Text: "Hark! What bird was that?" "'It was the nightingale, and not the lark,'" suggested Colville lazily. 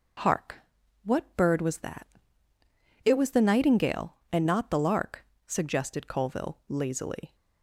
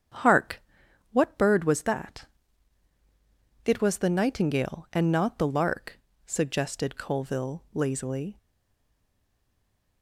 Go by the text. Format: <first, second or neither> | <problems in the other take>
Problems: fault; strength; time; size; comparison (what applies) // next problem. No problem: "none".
first | starts louder than the rest; strong; until 1.6 s; 8 dB // stays silent after the last word; noticeable; from 8.3 s on; 1.7 s long